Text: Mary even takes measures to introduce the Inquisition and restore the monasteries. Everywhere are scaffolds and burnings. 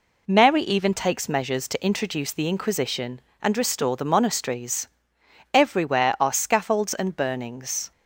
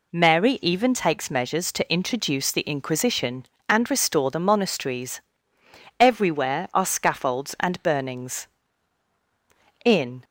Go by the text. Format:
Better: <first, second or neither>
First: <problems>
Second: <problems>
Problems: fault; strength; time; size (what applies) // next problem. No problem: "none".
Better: first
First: none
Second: goes on to say "In"; slight; from 9.8 s on; 0.40 s long